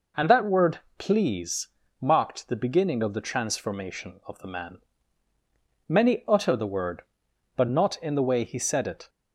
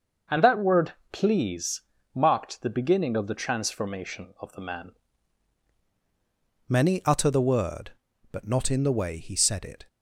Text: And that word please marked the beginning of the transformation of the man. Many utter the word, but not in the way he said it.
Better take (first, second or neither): first